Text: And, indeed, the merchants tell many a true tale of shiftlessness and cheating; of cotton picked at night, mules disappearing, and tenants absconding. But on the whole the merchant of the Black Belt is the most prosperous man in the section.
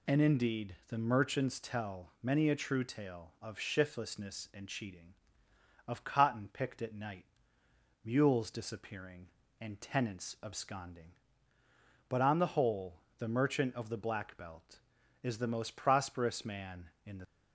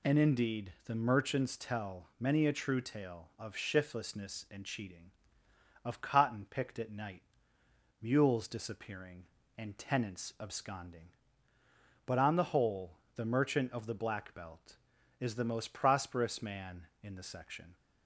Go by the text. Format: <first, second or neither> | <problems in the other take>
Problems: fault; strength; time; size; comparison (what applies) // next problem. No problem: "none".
second | pauses between "whole" and "the"; slight; at 12.9 s; 0.18 s long; slight in the second // stops before "section"; at 17.2 s